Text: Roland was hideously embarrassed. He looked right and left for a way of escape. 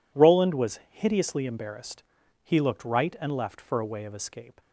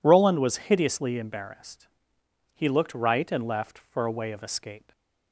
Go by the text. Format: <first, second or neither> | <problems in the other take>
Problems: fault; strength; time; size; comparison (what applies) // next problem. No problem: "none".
neither | none